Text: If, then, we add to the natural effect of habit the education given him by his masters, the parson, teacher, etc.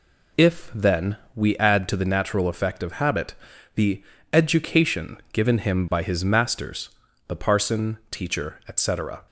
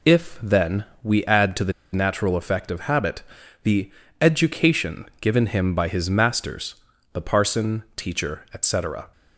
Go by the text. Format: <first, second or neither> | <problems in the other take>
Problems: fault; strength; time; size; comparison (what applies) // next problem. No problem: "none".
first | pauses between "the" and "natural"; slight; at 1.7 s; 0.21 s long // pauses between "habit" and "the"; at 3.2 s; 0.42 s long; also in the first // pauses between "the" and "education"; slight; at 3.8 s; 0.30 s long; slight in the first